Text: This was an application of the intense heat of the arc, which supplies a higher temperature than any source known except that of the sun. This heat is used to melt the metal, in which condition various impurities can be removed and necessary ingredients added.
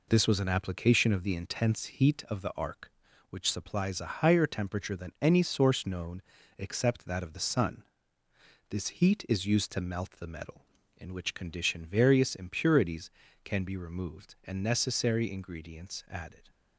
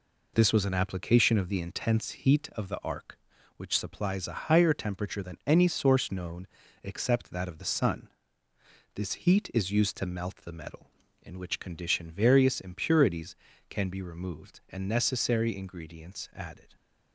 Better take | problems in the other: neither | pauses between "known" and "except"; slight; the same in both

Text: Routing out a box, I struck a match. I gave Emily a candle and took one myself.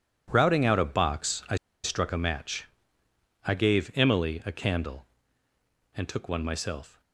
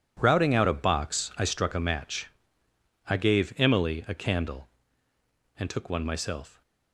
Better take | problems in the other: second | pauses between "I" and "struck"; slight; at 1.5 s; 0.29 s long

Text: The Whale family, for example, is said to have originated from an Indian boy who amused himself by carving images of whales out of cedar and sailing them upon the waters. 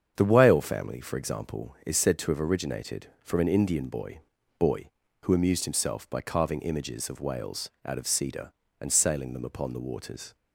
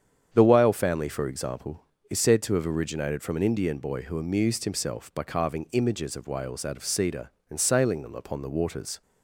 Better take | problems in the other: second | starts louder than the rest; strong; until 1.1 s; 7.5 dB; strong in the second // says "boy" twice; at 4.5 s // pauses between "whales" and "out"; slight; at 7.6 s; 0.16 s long

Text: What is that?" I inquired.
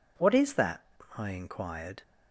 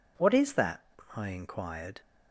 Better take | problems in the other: neither | none

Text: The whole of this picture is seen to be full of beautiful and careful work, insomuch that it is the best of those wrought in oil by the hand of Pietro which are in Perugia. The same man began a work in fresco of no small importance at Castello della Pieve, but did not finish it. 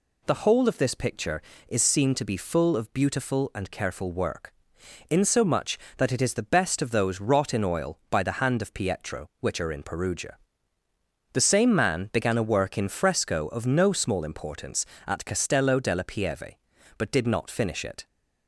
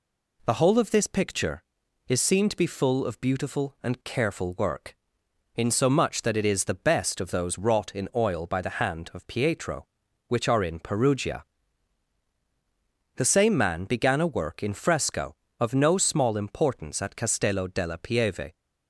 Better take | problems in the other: first | stops before "but did not finish it"; at 18.5 s

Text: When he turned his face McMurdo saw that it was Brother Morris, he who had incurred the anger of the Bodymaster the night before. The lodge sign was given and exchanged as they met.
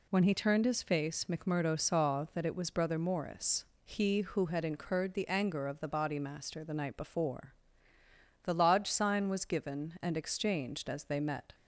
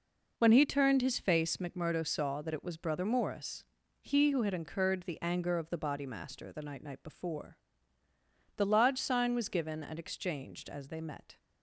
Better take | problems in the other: first | says "night" twice; at 6.8 s

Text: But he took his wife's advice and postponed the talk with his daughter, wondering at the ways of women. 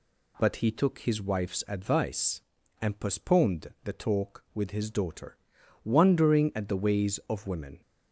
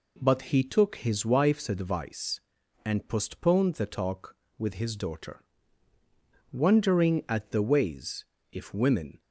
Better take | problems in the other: first | says "if" for "of"; at 8.5 s

